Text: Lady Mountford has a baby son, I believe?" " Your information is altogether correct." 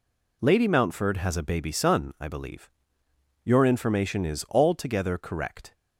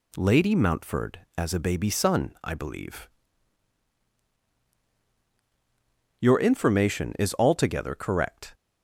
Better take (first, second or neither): first